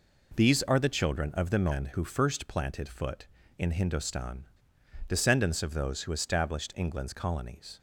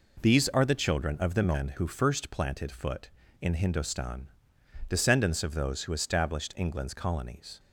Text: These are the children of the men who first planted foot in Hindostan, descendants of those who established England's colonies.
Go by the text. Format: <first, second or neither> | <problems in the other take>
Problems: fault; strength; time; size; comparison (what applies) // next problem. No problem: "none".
neither | none